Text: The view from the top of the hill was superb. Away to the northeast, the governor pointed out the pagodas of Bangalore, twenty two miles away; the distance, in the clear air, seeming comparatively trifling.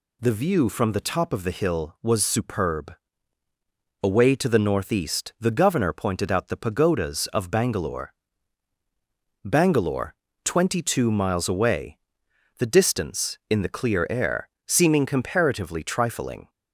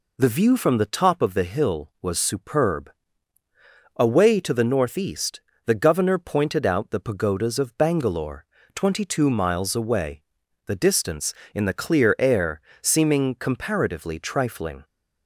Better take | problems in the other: second | says "Bangalore" twice; at 9.4 s

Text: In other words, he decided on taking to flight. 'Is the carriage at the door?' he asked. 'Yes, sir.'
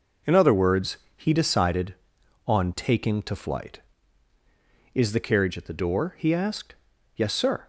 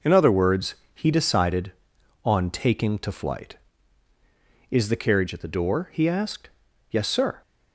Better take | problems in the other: neither | none

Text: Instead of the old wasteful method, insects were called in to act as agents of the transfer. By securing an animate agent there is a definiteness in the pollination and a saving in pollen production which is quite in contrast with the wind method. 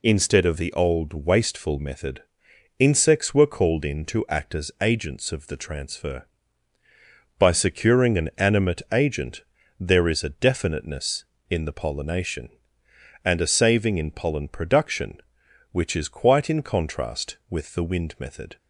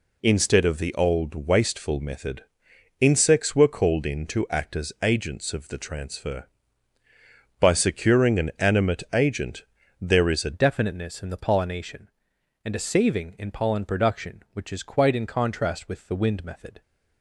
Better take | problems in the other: first | pauses between "agent" and "there"; slight; at 9.6 s; 0.36 s long; slight in the first // changes voice at "definiteness"; from 10.5 s on; 6.3 s long

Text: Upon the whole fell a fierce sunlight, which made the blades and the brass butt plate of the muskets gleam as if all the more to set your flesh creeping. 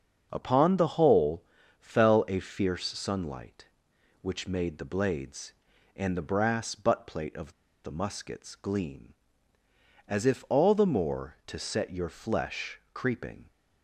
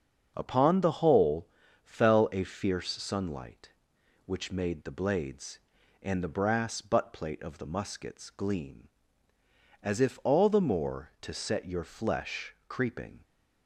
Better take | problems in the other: second | starts louder than the rest; until 1.3 s; 6.5 dB; also in the second // pauses between "whole" and "fell"; at 1.4 s; 0.38 s long; also in the second // pauses between "of" and "the"; slight; at 7.5 s; 0.32 s long // pauses between "flesh" and "creeping"; slight; at 12.7 s; 0.16 s long; slight in the second

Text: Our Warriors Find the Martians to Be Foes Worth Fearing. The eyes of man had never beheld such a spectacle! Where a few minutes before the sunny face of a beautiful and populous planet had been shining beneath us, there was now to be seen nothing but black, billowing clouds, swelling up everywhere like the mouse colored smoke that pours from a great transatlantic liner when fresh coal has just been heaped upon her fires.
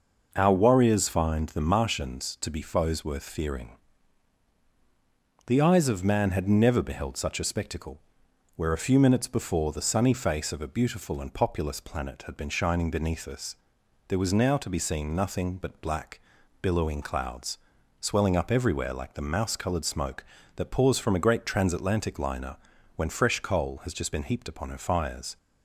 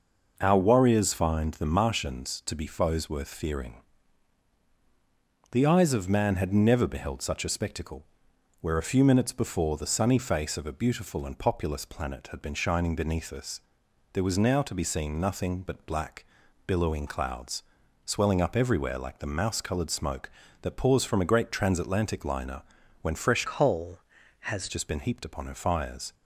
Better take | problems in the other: first | pauses between "liner" and "when"; at 22.6 s; 0.38 s long; also in the first // changes voice from "coal" to "has"; from 23.4 to 24.6 s; 1.2 s long

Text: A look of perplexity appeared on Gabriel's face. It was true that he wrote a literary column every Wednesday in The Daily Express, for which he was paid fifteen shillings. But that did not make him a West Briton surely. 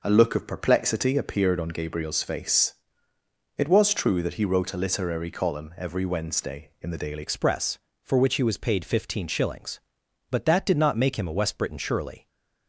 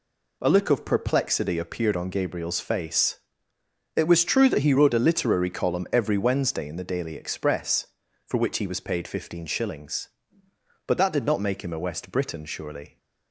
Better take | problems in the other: second | changes voice at "Express"; from 7.2 s on; 5.0 s long // stays silent after the last word; slight; from 12.1 s on; 0.5 s long

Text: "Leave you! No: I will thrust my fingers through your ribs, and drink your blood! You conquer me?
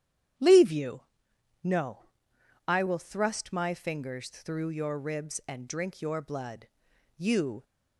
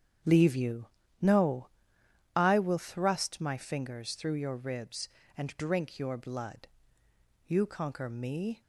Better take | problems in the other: second | starts louder than the rest; strong; until 2.0 s; 10 dB; strong in the second // stops before "conquer me"; at 7.6 s

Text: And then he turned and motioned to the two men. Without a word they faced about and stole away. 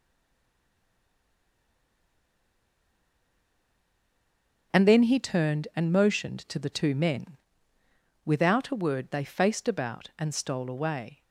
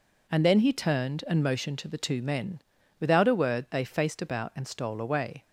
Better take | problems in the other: second | stays silent before the first word; strong; until 4.7 s; 4.7 s long // starts louder than the rest; noticeable; until 5.8 s; 6 dB

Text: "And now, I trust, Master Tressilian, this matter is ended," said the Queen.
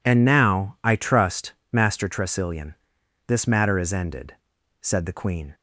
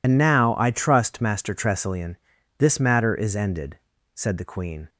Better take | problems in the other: first | loses the start of "And"; at 0.0 s; 75 ms

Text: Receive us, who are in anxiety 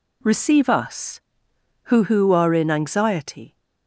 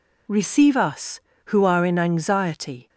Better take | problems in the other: second | says "who" twice; at 2.0 s

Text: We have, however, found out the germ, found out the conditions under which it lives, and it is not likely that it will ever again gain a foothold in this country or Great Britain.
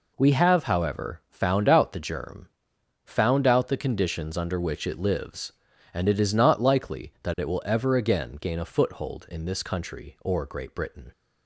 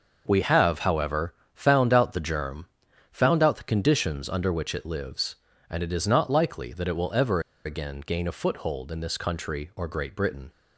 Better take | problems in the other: first | pauses between "ever" and "again"; slight; at 7.4 s; 0.24 s long

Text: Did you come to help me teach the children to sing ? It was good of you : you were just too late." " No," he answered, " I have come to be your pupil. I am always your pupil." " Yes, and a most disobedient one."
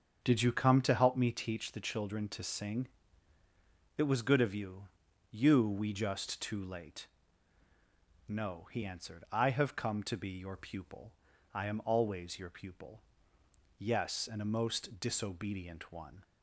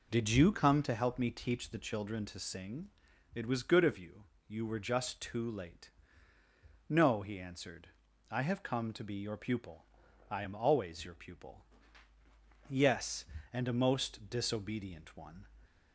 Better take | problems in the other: second | starts louder than the rest; strong; until 1.2 s; 7 dB // says "we" for "were"; at 5.6 s

